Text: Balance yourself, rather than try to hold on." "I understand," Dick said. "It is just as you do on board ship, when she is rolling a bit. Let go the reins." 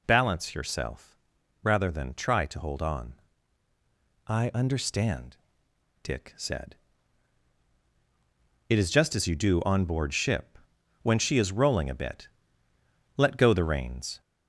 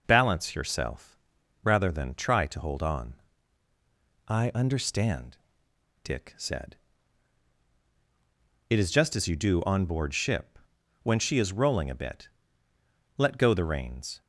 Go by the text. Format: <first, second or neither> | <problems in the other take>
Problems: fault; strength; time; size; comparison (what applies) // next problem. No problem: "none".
second | gets louder; slight; throughout; 2.5 dB